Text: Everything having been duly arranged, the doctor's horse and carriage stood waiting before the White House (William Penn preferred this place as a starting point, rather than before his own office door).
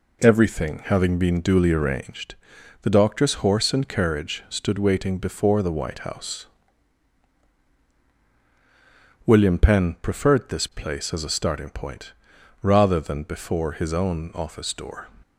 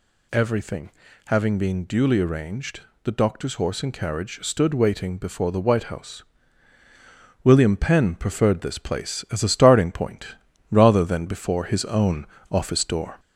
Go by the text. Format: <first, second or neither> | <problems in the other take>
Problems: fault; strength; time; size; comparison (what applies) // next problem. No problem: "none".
first | gets louder; slight; throughout; 2.5 dB // pauses between "Everything" and "having"; slight; at 0.9 s; 0.36 s long // pauses between "own" and "office"; slight; at 12.2 s; 0.26 s long